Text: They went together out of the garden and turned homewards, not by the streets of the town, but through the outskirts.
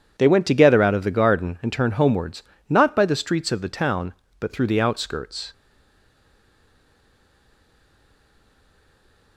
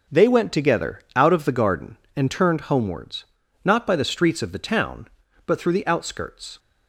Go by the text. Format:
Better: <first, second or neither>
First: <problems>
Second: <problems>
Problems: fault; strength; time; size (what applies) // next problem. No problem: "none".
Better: second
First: stays silent after the last word; strong; from 5.5 s on; 3.8 s long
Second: none